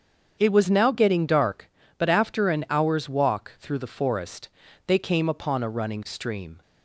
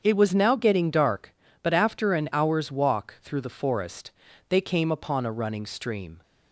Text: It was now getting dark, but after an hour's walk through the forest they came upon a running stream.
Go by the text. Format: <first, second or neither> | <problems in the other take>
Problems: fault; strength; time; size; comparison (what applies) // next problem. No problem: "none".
neither | starts louder than the rest; strong; the same in both // pauses between "forest" and "they"; slight; the same in both